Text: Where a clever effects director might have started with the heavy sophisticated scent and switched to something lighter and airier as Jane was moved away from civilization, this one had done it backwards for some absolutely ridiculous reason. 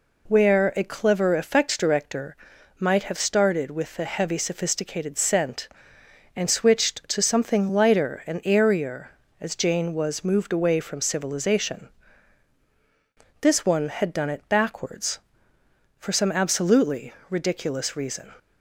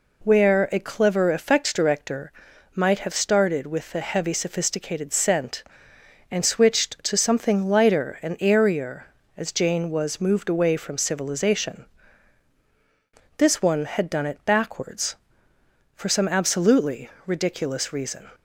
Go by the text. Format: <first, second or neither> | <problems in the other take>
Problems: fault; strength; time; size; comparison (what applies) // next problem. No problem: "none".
neither | pauses between "director" and "might"; noticeable; the same in both // pauses between "absolutely" and "ridiculous"; slight; the same in both